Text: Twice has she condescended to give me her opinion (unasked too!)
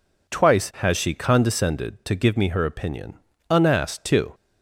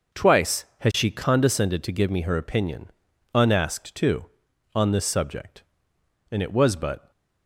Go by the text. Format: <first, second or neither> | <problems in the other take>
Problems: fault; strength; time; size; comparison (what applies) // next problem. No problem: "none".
first | goes on to say "on this subject and it was but"; strong; from 4.7 s on; 2.3 s long